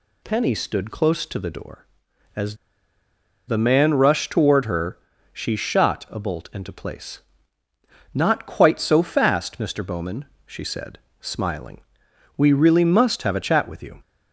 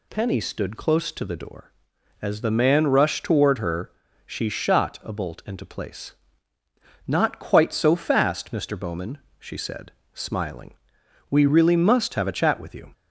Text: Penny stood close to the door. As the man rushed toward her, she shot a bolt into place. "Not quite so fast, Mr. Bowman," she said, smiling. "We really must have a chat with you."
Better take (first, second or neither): second